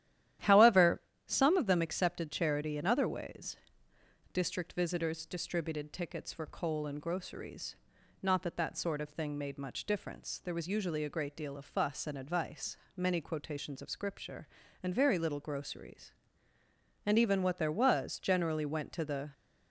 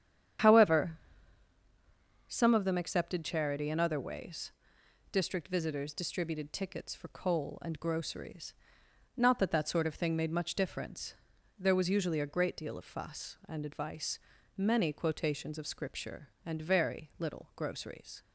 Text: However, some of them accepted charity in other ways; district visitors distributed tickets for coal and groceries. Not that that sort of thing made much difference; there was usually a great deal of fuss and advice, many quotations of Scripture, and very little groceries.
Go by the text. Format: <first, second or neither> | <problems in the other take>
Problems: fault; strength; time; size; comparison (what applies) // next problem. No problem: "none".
second | starts louder than the rest; strong; until 1.6 s; 12 dB; strong in the second // goes on to say "And even what there was generally went to the"; strong; from 17.0 s on; 2.2 s long